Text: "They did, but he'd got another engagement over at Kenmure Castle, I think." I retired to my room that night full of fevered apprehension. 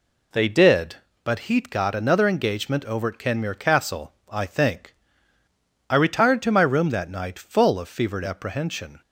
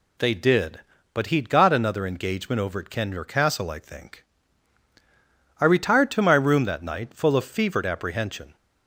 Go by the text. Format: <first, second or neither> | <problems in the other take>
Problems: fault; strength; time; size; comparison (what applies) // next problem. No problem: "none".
neither | none